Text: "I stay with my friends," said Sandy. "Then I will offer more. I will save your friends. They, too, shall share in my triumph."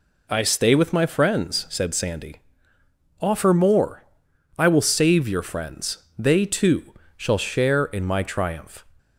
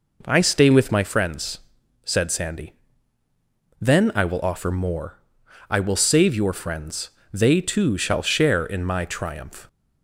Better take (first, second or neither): second